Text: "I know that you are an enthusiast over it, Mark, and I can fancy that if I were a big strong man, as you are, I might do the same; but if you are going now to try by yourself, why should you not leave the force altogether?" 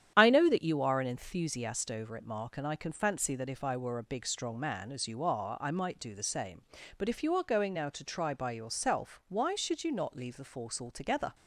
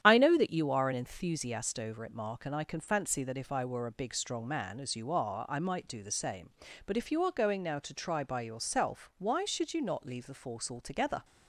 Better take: neither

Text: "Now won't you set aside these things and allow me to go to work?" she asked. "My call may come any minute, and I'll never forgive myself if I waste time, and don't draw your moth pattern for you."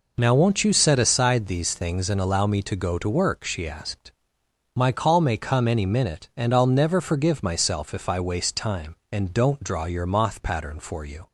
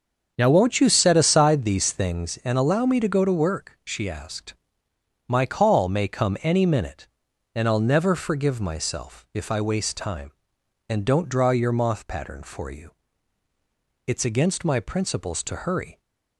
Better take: first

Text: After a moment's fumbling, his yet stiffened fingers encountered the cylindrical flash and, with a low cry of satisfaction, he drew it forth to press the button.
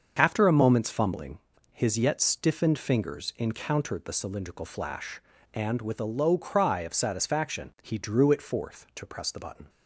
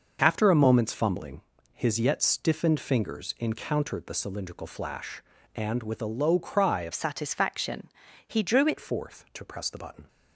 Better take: first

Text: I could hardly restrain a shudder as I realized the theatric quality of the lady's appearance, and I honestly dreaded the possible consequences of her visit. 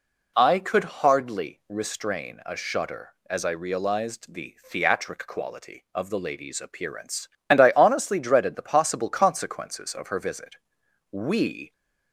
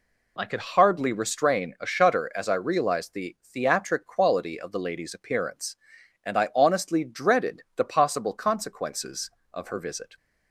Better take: second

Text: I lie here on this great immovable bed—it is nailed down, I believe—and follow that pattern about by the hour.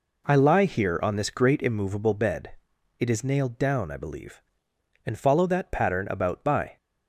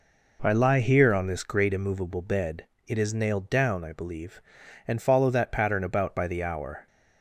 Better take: second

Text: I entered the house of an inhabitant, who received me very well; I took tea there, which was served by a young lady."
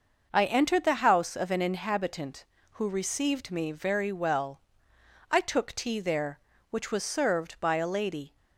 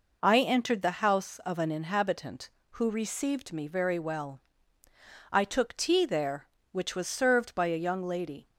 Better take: second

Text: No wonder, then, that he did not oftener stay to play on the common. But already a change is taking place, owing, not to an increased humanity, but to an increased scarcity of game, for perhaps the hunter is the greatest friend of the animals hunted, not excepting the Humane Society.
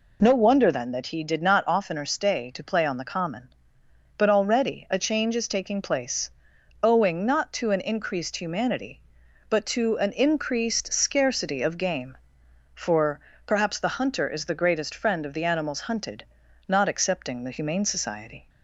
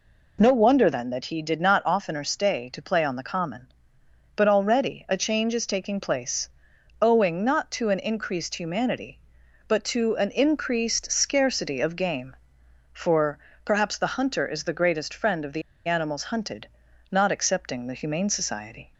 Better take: first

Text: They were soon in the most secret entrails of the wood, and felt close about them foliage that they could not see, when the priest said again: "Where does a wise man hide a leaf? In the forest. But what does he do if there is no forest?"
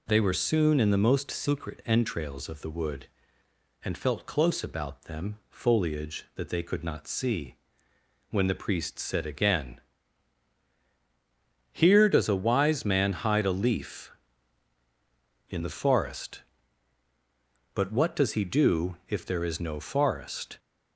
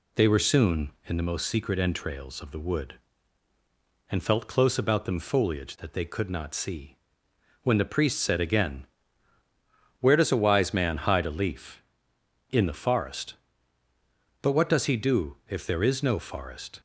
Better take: second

